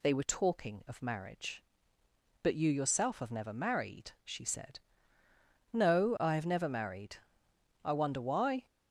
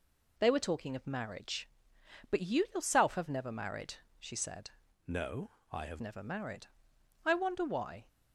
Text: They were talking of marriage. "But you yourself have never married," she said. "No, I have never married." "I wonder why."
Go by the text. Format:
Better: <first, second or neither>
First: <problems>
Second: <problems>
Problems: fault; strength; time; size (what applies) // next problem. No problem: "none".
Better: first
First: none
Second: changes voice from "No" to "have"; from 5.0 to 6.0 s; 1.0 s long